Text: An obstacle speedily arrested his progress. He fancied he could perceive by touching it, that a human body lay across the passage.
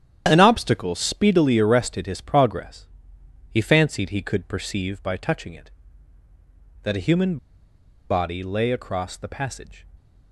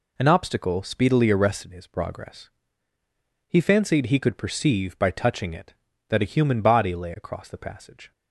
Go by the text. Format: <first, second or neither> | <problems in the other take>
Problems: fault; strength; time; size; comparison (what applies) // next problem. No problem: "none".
second | starts louder than the rest; strong; until 1.2 s; 10 dB // pauses between "human" and "body"; noticeable; at 7.3 s; 0.73 s long